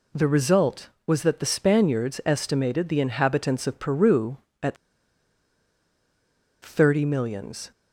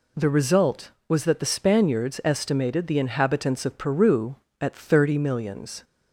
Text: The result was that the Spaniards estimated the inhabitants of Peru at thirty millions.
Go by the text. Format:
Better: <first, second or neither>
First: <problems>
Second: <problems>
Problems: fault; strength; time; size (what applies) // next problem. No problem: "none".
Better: second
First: pauses between "at" and "thirty"; strong; at 4.7 s; 1.8 s long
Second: none